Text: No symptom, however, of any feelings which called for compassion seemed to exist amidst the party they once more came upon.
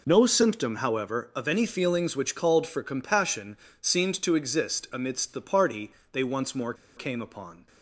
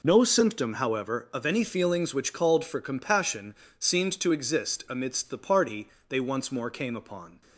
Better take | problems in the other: second | pauses between "compassion" and "seemed"; slight; at 3.5 s; 0.24 s long; slight in the second // pauses between "party" and "they"; slight; at 5.9 s; 0.20 s long; slight in the second // pauses between "more" and "came"; slight; at 6.7 s; 0.22 s long

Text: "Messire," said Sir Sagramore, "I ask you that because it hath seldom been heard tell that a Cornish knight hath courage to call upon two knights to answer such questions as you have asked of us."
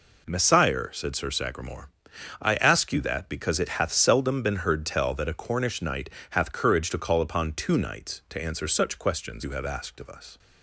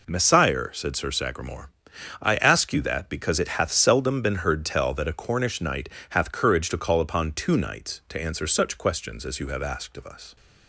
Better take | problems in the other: second | pauses between "knight" and "hath"; slight; at 6.0 s; 0.22 s long; slight in the second // skips "as"; at 9.4 s

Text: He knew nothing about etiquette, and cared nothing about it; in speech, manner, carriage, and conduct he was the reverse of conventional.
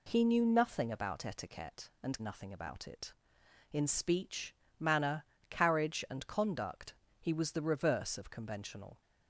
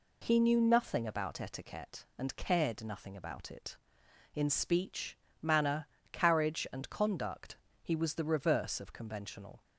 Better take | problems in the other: second | skips "cared"; at 2.2 s // pauses between "conduct" and "he"; slight; at 6.9 s; 0.24 s long; slight in the second

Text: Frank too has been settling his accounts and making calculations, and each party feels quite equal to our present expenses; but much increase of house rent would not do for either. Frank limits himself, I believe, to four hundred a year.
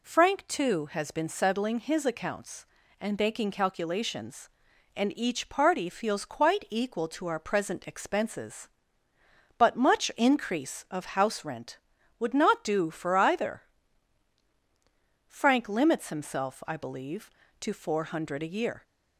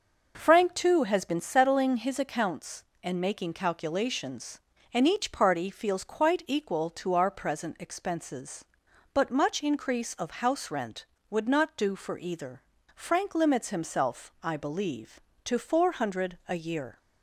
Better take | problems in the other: neither | none

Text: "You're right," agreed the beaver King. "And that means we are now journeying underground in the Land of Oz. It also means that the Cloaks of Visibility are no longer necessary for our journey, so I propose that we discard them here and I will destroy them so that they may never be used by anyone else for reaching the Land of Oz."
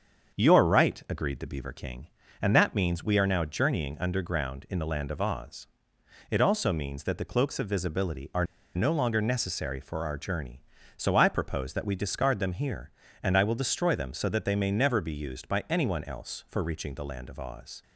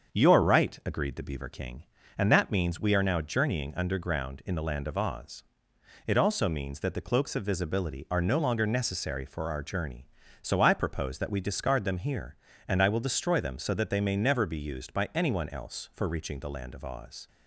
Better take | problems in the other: second | starts louder than the rest; until 1.4 s; 7 dB; also in the second // pauses between "are" and "no"; slight; at 8.4 s; 0.30 s long

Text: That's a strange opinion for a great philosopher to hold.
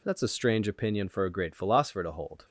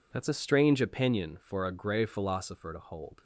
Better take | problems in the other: first | says "grey" for "great"; at 1.7 s

